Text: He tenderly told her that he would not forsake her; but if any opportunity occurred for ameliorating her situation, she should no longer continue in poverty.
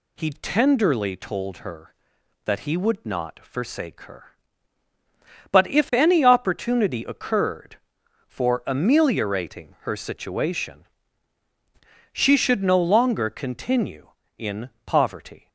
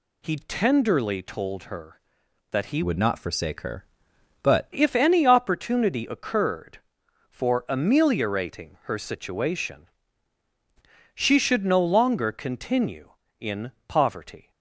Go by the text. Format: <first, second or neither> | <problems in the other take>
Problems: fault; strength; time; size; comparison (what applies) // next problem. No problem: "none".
first | changes voice from "would" to "but"; from 2.8 to 4.7 s; 1.9 s long // pauses between "in" and "poverty"; slight; at 13.6 s; 0.16 s long; slight in the first